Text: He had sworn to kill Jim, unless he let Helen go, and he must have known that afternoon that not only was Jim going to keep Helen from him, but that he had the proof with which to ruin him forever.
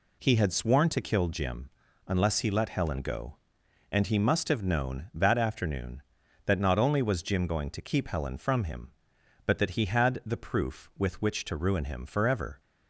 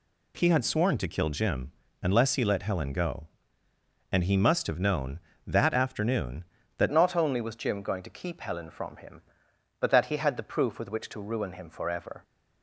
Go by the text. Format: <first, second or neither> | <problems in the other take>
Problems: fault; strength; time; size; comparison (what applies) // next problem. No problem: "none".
first | changes voice at "not"; from 6.9 s on; 5.3 s long